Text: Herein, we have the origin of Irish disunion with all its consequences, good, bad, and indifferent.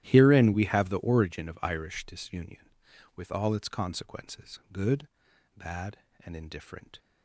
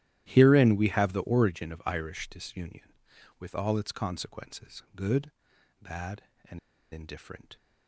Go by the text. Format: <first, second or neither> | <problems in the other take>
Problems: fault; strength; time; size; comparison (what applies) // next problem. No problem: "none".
first | starts louder than the rest; strong; until 1.2 s; 13.5 dB; strong in the first // pauses between "and" and "indifferent"; slight; at 6.5 s; 0.32 s long